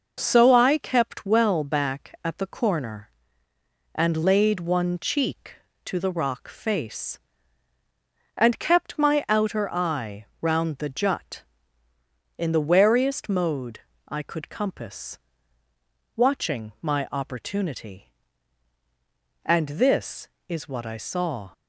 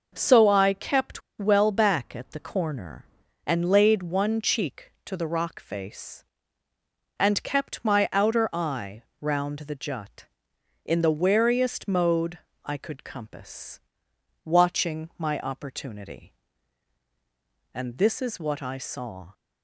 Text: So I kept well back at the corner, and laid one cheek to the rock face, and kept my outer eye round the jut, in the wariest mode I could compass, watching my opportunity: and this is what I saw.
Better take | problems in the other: first | pauses between "kept" and "well"; slight; at 1.2 s; 0.19 s long // pauses between "eye" and "round"; slight; at 9.0 s; 0.16 s long; slight in the first // pauses between "mode" and "I"; slight; at 12.3 s; 0.24 s long; slight in the first

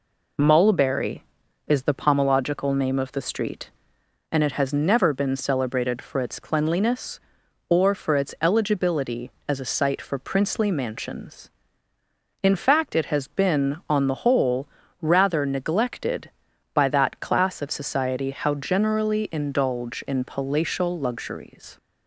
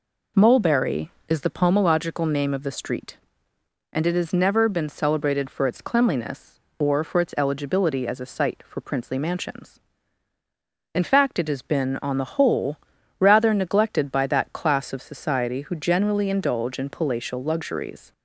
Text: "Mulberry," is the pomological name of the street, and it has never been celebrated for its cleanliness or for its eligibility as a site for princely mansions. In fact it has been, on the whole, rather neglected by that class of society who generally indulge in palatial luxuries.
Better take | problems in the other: second | says "how" for "who"; at 18.3 s

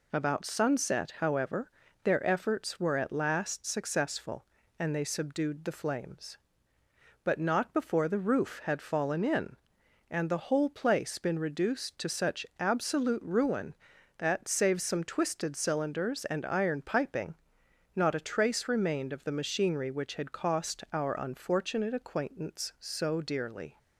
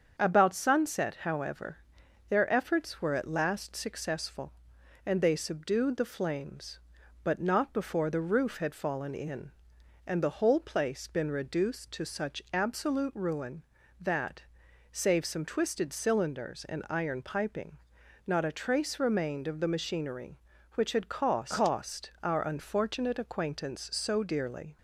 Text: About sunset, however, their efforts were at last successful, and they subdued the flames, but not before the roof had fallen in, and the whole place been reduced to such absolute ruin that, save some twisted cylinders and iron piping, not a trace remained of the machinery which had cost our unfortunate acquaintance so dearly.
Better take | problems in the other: first | starts louder than the rest; strong; until 1.2 s; 7 dB // says "cost" twice; at 21.5 s

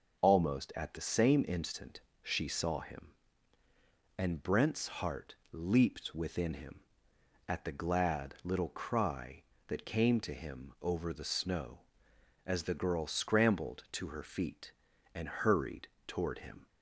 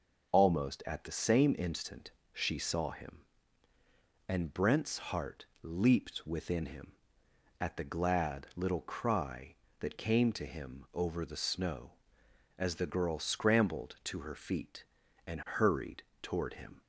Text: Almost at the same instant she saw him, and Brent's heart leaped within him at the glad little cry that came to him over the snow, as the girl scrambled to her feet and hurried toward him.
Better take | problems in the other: neither | pauses between "instant" and "she"; slight; the same in both // pauses between "heart" and "leaped"; slight; the same in both // pauses between "hurried" and "toward"; slight; the same in both

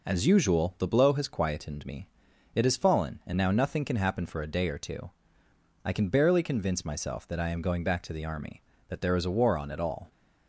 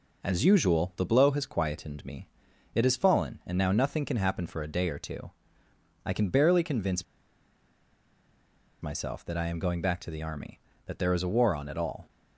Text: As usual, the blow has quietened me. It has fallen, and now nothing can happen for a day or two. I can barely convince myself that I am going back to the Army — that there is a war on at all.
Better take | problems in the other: first | pauses between "convince" and "myself"; strong; at 7.0 s; 1.7 s long

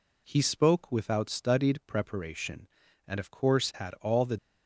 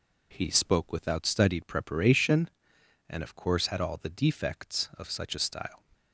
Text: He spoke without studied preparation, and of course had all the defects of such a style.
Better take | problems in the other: second | stops before "defects of such a style"; at 4.3 s

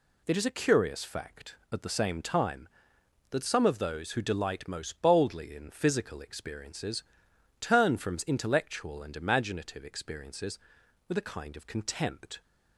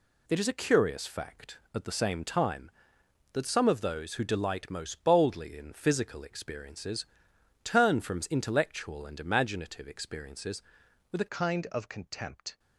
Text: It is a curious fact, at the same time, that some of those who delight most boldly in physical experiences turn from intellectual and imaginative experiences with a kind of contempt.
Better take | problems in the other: first | pauses between "experiences" and "turn"; noticeable; at 7.0 s; 0.56 s long; noticeable in the first // changes voice at "kind"; from 11.2 s on; 1.3 s long

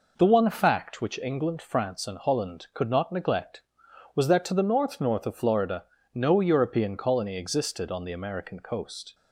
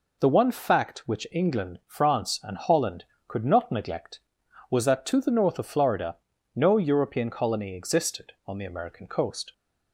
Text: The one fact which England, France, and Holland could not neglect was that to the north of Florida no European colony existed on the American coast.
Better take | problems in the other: second | says "north" twice; at 5.0 s // pauses between "Florida" and "no"; slight; at 5.8 s; 0.32 s long; also in the second

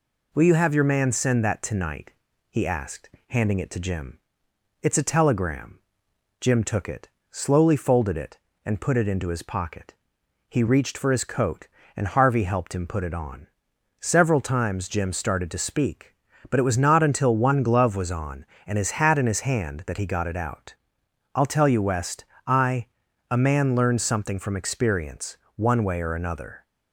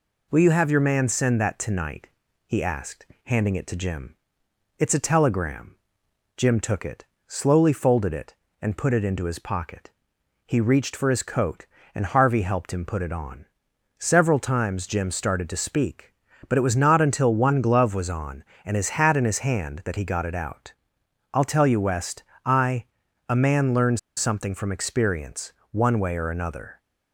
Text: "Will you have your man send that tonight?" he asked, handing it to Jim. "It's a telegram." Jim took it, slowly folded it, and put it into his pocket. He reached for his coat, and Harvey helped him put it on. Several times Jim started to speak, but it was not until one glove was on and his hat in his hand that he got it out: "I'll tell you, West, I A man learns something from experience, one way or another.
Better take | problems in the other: first | pauses between "I" and "A"; noticeable; at 22.8 s; 0.46 s long; noticeable in the first // pauses between "learns" and "something"; slight; at 23.9 s; 0.19 s long

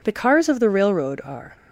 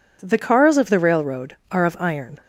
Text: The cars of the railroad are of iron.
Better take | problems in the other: second | stops before "of iron"; at 1.5 s

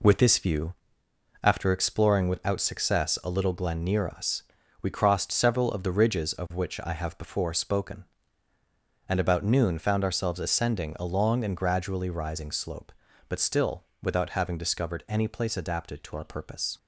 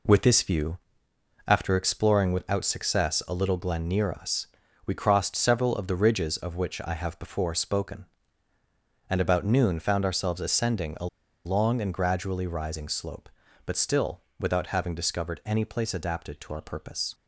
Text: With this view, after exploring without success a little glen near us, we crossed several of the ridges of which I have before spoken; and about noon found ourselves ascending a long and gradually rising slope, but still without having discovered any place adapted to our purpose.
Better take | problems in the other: first | pauses between "a" and "long"; at 11.0 s; 0.39 s long // pauses between "still" and "without"; slight; at 14.2 s; 0.20 s long; slight in the first

